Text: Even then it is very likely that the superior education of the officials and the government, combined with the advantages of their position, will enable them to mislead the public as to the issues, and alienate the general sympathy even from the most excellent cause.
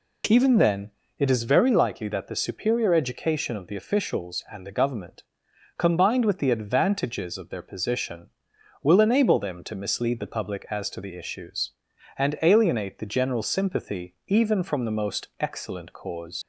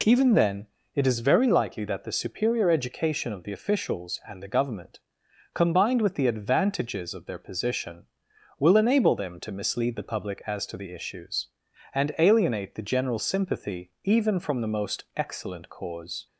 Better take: second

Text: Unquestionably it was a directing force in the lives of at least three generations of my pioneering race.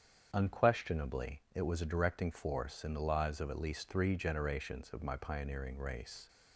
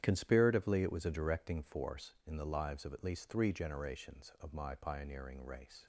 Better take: first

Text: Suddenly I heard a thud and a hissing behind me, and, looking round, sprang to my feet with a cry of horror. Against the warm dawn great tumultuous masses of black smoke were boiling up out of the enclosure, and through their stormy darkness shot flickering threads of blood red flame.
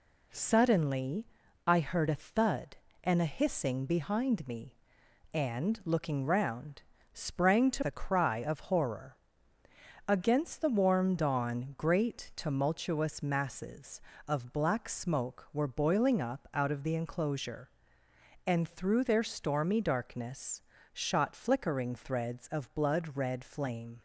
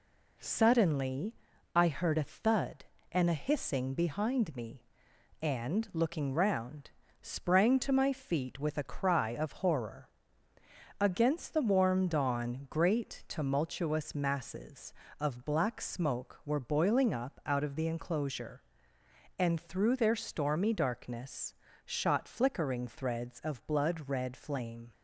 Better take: second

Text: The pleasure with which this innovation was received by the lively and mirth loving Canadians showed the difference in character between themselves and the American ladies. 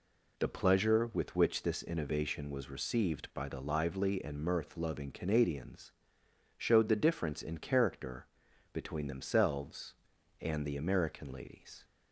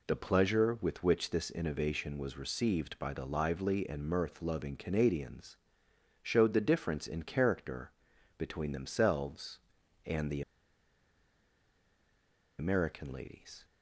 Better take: first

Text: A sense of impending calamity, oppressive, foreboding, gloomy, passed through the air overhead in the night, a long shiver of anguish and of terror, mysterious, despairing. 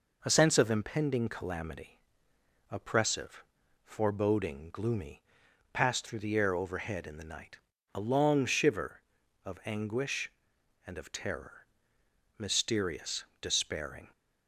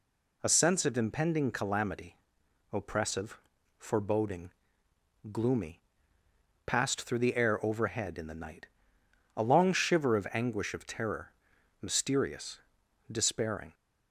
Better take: first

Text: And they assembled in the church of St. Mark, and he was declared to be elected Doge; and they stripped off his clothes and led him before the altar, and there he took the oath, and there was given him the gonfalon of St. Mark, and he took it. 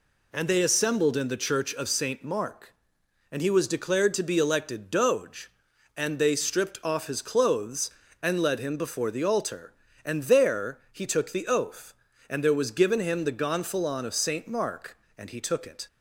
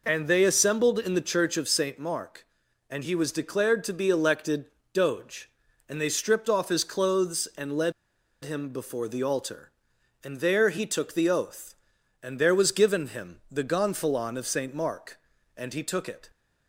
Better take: first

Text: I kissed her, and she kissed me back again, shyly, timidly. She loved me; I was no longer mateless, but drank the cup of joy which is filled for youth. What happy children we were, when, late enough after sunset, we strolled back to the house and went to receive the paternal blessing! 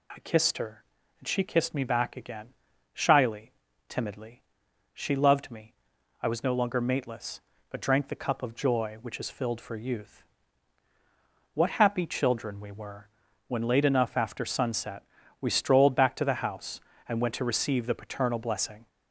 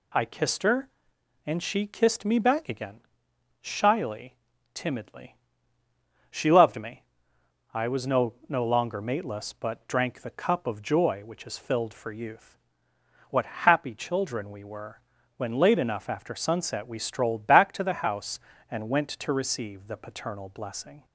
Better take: first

